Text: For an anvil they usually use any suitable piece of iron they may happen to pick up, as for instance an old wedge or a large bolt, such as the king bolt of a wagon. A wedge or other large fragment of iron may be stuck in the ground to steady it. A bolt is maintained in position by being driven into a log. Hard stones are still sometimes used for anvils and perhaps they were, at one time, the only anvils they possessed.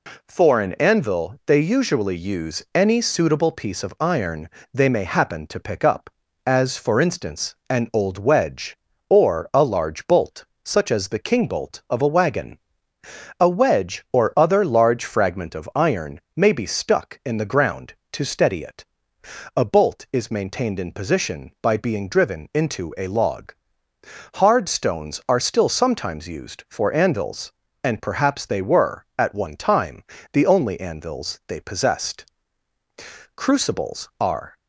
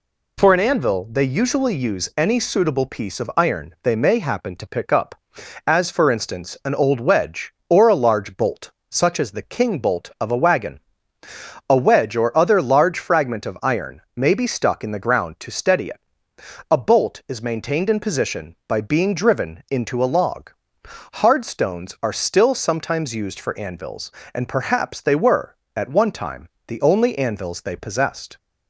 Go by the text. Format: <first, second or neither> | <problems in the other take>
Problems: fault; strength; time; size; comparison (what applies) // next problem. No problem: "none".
second | pauses between "iron" and "they"; slight; at 4.4 s; 0.22 s long // pauses between "instance" and "an"; slight; at 7.5 s; 0.16 s long // goes on to say "Crucibles are"; noticeable; from 33.3 s on; 1.2 s long